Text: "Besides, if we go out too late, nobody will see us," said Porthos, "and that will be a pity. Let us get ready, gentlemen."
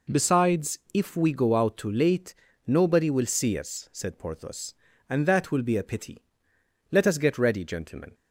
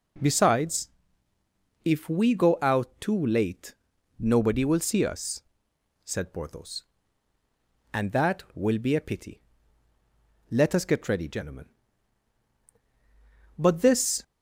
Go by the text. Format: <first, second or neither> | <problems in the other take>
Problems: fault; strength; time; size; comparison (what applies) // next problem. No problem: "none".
first | goes on to say "But this"; noticeable; from 13.5 s on; 0.64 s long